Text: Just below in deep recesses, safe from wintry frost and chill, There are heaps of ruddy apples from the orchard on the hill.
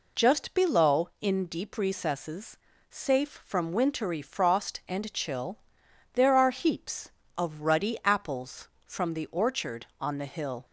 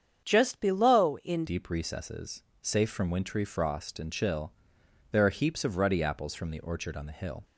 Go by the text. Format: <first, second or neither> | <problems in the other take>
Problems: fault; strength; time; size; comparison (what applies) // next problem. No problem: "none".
first | starts louder than the rest; strong; until 1.2 s; 8 dB // changes voice at "deep"; from 1.4 s on; 6.0 s long